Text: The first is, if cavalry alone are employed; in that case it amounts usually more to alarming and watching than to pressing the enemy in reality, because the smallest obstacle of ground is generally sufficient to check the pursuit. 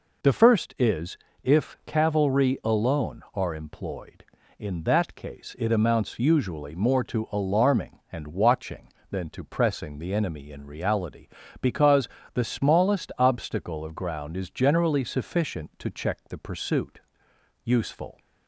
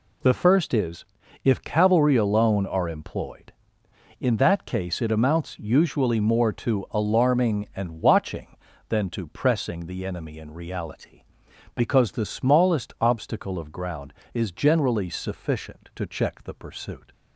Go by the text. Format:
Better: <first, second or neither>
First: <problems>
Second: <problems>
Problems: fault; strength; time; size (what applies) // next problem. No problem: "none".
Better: second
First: pauses between "because" and "the"; slight; at 12.0 s; 0.24 s long // goes on to say "Useful"; from 17.6 s on; 0.56 s long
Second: none